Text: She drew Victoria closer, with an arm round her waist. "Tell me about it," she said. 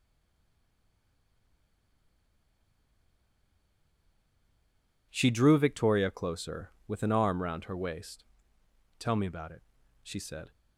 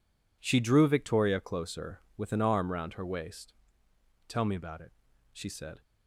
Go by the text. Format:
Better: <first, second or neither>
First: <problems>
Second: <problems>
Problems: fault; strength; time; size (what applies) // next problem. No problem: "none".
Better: second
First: stays silent before the first word; strong; until 5.0 s; 5.0 s long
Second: none